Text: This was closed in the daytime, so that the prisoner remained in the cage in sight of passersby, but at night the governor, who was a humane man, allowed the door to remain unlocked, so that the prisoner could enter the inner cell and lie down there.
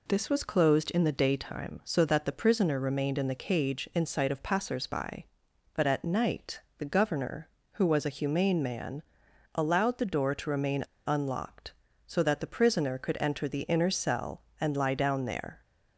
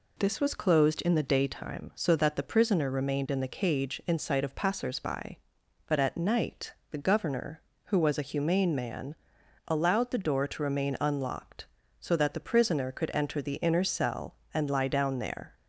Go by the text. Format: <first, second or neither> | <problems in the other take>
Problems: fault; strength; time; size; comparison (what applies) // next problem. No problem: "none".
second | pauses between "night" and "the"; slight; at 6.6 s; 0.16 s long; slight in the second // pauses between "remain" and "unlocked"; slight; at 10.8 s; 0.21 s long